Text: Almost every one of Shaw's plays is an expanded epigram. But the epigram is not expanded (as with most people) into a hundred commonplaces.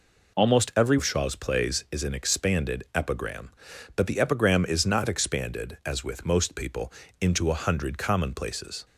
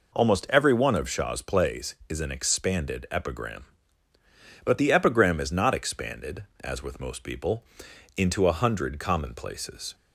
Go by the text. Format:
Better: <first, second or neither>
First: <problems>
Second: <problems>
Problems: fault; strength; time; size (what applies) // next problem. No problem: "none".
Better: second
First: skips "one"; at 0.9 s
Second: none